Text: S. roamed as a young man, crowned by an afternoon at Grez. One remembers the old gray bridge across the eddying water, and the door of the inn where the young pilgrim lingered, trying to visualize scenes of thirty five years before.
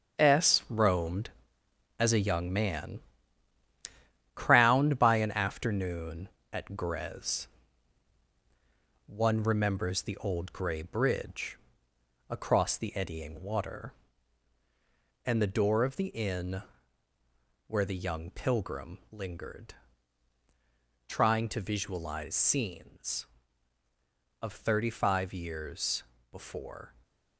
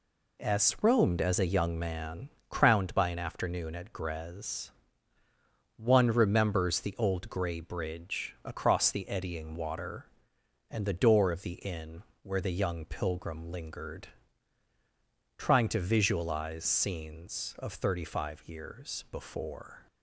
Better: second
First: gets quieter; strong; throughout; 8.5 dB // pauses between "bridge" and "across"; noticeable; at 11.5 s; 0.72 s long // pauses between "inn" and "where"; at 16.6 s; 1.0 s long // pauses between "years" and "before"; slight; at 26.0 s; 0.26 s long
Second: pauses between "inn" and "where"; slight; at 12.0 s; 0.18 s long

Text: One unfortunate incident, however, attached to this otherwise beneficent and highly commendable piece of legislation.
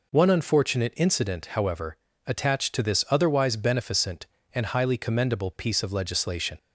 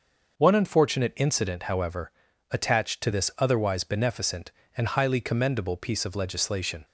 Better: neither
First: none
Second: none

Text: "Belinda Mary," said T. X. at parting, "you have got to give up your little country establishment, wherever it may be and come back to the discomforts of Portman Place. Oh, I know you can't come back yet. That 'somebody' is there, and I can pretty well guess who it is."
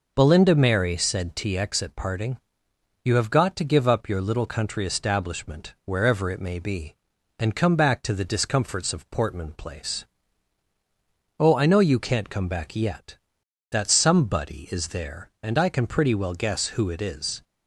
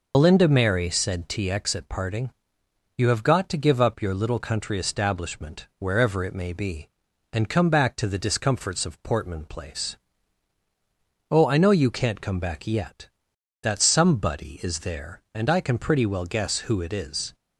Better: first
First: none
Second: loses the start of "Belinda"; at 0.1 s; 60 ms

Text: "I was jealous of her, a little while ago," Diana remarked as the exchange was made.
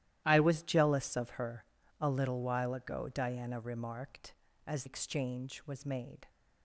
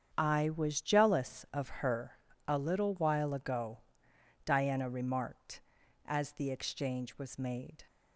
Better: second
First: starts louder than the rest; strong; until 1.2 s; 13.5 dB // skips "the"; at 4.8 s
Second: starts louder than the rest; strong; until 1.1 s; 8 dB

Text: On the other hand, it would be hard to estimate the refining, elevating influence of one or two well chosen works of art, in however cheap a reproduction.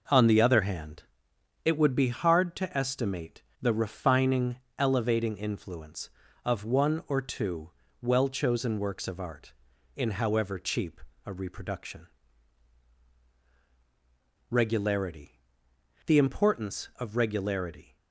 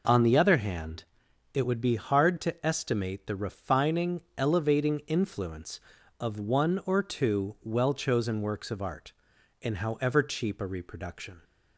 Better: second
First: pauses between "estimate" and "the"; slight; at 3.4 s; 0.18 s long // pauses between "two" and "well"; slight; at 7.7 s; 0.30 s long // pauses between "cheap" and "a"; slight; at 11.0 s; 0.24 s long // goes on to say "Regularity The importance of Regularity"; strong; from 14.4 s on; 3.4 s long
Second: none

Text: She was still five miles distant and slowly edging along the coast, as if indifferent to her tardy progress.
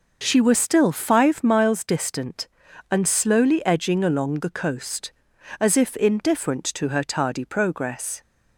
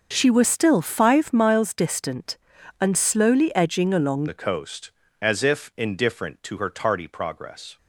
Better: first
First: none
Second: starts louder than the rest; noticeable; until 1.1 s; 6 dB // changes voice at "the"; from 4.2 s on; 3.5 s long

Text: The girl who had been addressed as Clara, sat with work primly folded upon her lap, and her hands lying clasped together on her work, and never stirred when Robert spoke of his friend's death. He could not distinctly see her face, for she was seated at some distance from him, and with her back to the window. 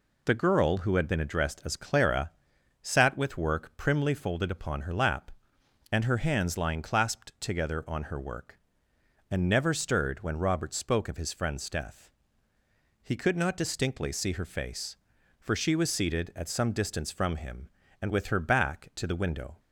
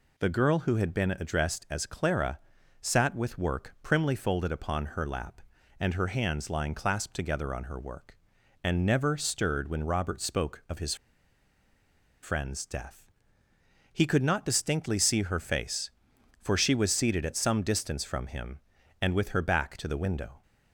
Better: first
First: none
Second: pauses between "his" and "friend's"; strong; at 10.9 s; 1.2 s long

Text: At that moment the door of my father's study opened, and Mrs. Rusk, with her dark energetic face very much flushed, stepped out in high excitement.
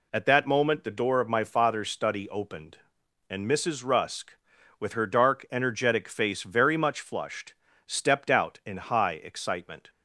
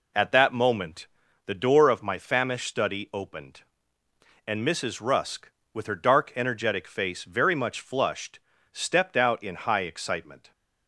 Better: first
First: none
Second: pauses between "moment" and "the"; at 1.0 s; 0.38 s long // says "famished" for "father's"; at 2.1 s

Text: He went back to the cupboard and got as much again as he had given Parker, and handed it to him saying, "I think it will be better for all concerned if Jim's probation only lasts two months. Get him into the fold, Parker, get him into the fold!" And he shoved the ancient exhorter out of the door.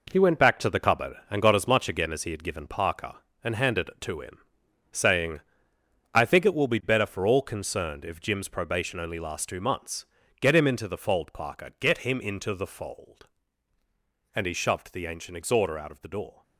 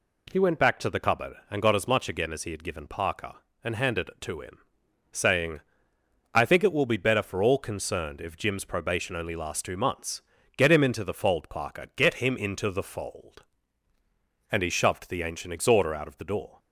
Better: second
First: gets quieter; strong; throughout; 8.5 dB // pauses between "him" and "saying"; noticeable; at 4.3 s; 0.52 s long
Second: pauses between "him" and "saying"; noticeable; at 4.5 s; 0.52 s long

